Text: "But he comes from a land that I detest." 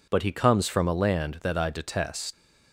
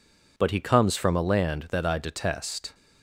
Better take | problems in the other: second | leaves "detest" unfinished; at 2.3 s; 125 ms

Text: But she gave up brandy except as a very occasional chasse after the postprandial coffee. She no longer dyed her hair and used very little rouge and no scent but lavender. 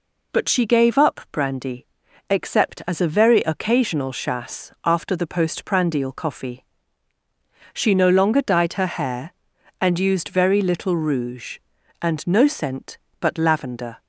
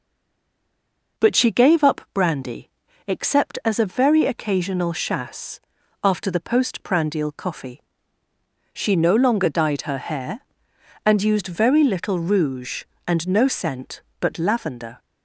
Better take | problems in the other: first | stays silent before the first word; noticeable; until 1.1 s; 1.1 s long // pauses between "brandy" and "except"; at 2.7 s; 0.38 s long; noticeable in the first // pauses between "chasse" and "after"; at 5.6 s; 0.42 s long; slight in the first

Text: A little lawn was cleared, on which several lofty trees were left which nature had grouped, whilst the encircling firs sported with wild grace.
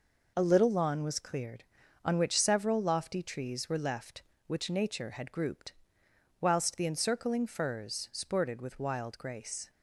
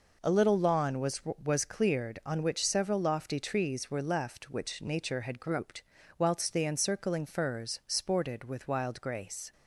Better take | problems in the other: first | says "was" twice; at 1.4 s

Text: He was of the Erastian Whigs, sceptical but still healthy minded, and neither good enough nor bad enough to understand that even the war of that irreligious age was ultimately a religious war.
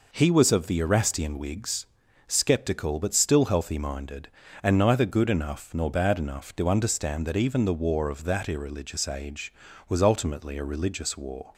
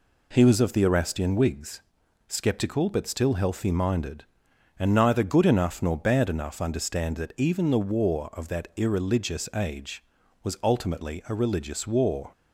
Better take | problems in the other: first | skips "to"; at 6.6 s

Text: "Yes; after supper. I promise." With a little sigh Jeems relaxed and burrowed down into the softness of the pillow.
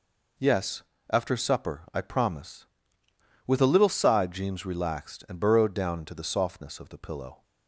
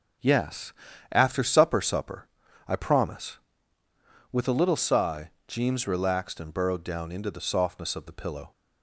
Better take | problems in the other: first | starts louder than the rest; strong; until 1.6 s; 8.5 dB // says "supper" twice; at 1.7 s // pauses between "sigh" and "Jeems"; slight; at 5.3 s; 0.16 s long

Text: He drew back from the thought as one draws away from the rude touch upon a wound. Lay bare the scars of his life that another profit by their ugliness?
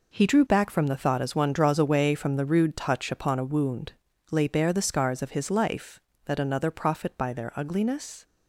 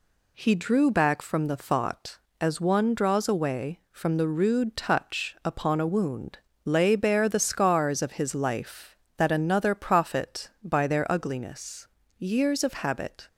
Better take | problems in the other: first | goes on to say "Years of habit"; noticeable; from 12.1 s on; 1.1 s long

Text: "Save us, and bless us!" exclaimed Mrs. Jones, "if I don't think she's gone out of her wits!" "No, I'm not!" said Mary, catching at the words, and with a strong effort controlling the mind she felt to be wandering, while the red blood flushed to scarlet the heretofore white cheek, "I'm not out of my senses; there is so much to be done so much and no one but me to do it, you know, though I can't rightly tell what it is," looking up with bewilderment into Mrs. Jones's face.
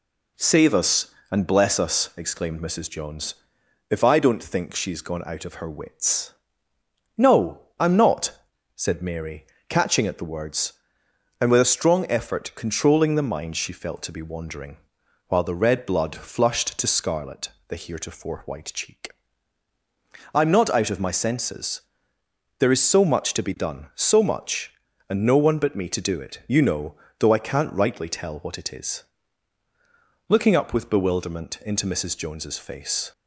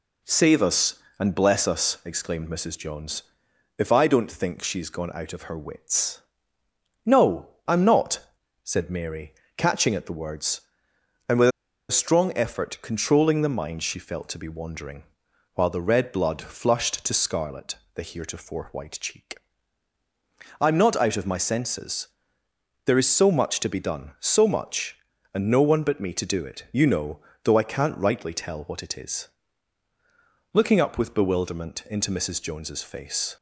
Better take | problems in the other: first | pauses between "with" and "a"; at 11.4 s; 0.41 s long // pauses between "scarlet" and "the"; slight; at 17.7 s; 0.18 s long; slight in the first

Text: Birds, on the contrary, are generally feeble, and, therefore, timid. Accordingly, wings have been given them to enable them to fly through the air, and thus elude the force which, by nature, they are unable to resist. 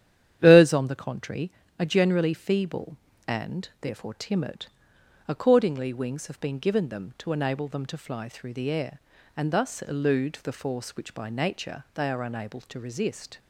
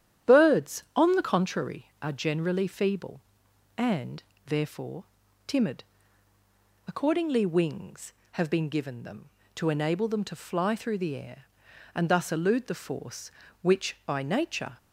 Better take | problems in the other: first | starts louder than the rest; strong; until 1.3 s; 10.5 dB; strong in the first // stops before "they are unable to resist"; at 14.7 s

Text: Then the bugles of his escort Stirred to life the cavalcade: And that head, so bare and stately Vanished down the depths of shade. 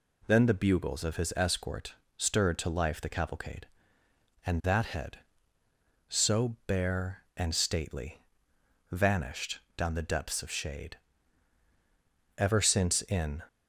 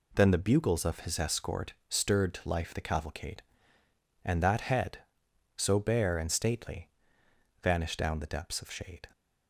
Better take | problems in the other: second | pauses between "escort" and "Stirred"; slight; at 1.9 s; 0.24 s long; slight in the second // pauses between "stately" and "Vanished"; noticeable; at 8.1 s; 0.72 s long; noticeable in the second // pauses between "Vanished" and "down"; slight; at 9.5 s; 0.18 s long // goes on to say "Ever since in"; noticeable; from 12.3 s on; 1.0 s long

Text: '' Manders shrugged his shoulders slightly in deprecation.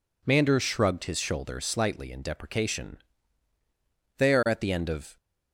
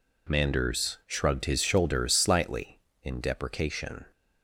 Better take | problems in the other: second | goes on to say "They are at the end of"; noticeable; from 4.1 s on; 0.98 s long

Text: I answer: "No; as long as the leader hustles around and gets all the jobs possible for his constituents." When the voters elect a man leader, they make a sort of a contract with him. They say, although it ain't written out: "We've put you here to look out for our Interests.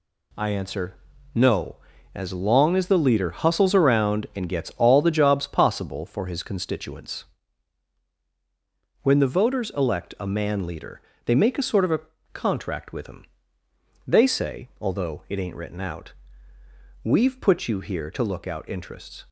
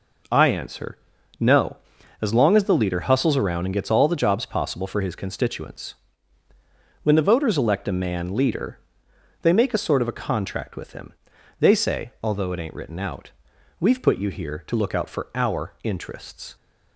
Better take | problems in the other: second | pauses between "a" and "contract"; slight; at 12.0 s; 0.32 s long // skips "for our"; at 18.6 s

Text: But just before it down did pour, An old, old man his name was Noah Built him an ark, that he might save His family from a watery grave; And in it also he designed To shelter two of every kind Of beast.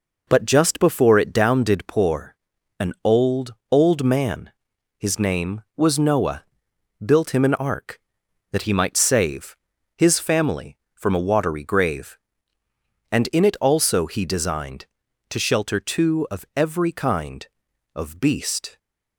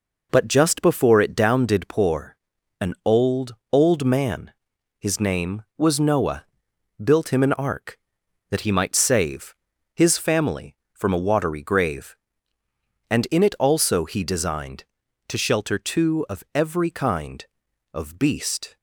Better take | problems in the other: neither | pauses between "man" and "his"; noticeable; the same in both // pauses between "Noah" and "Built"; noticeable; the same in both // pauses between "save" and "His"; the same in both

